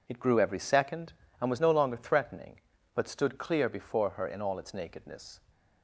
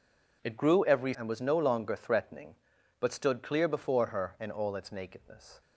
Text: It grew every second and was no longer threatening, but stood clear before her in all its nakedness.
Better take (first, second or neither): first